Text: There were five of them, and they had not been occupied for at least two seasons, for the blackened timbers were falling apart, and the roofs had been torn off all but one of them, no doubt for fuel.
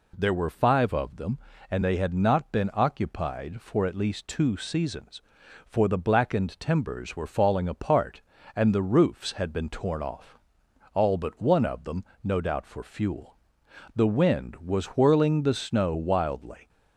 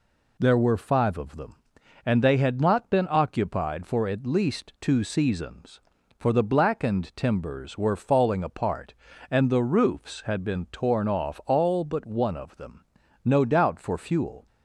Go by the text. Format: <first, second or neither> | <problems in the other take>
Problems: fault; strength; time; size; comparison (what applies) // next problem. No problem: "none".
second | pauses between "off" and "all"; noticeable; at 10.3 s; 0.58 s long // goes on to say "The wind was whirling the snow wildly"; strong; from 13.9 s on; 2.7 s long